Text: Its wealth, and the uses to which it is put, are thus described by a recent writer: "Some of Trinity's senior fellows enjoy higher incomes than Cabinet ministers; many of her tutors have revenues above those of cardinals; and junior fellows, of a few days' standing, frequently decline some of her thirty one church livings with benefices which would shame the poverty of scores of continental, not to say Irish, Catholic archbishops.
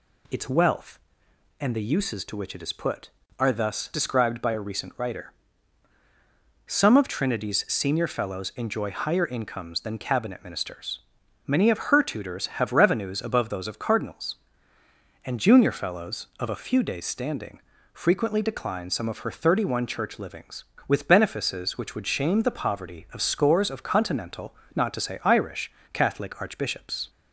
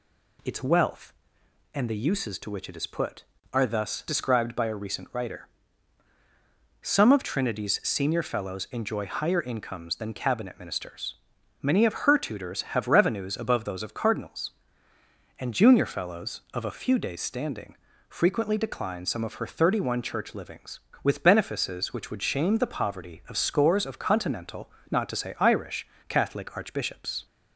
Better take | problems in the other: neither | none

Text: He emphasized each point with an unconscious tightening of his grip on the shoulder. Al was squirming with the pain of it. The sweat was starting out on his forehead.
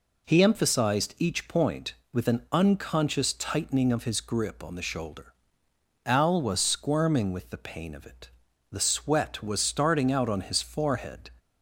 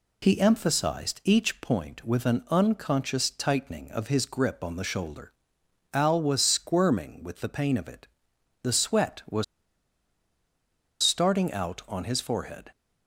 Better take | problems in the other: first | pauses between "was" and "starting"; strong; at 9.4 s; 1.5 s long

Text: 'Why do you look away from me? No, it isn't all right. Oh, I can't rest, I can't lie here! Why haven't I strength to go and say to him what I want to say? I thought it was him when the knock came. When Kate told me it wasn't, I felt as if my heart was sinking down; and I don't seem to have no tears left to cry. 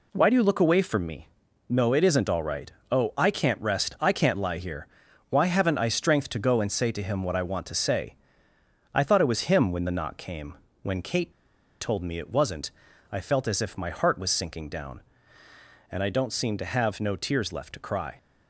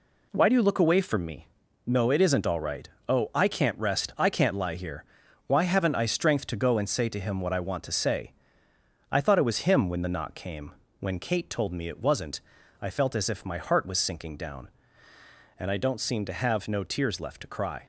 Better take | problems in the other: second | pauses between "Kate" and "told"; noticeable; at 11.3 s; 0.49 s long

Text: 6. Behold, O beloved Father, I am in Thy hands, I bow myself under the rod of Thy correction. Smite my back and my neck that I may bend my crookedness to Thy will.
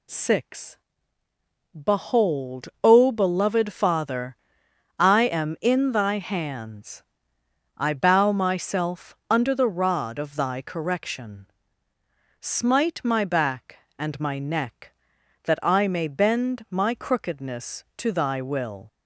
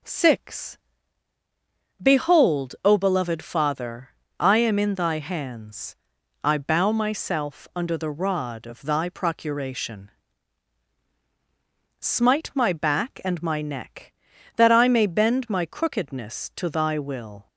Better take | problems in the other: first | says "procuration" for "correction"; at 9.0 s

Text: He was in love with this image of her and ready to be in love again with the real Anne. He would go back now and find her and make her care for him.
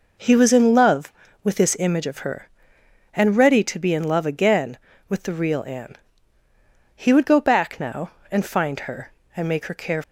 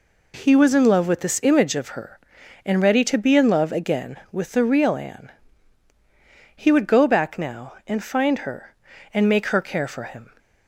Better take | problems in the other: second | stops before "for him"; at 10.0 s

